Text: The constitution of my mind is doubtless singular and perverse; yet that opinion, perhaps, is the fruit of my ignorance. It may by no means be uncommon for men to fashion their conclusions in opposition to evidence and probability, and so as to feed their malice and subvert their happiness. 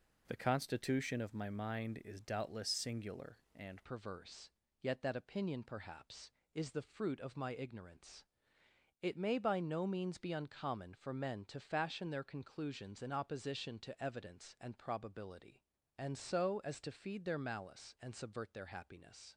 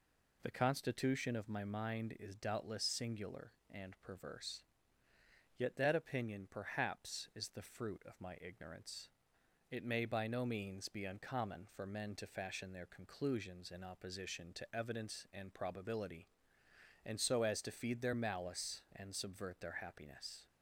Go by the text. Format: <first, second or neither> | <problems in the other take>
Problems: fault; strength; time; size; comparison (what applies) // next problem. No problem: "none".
second | changes voice at "perverse"; from 3.8 s on; 15.5 s long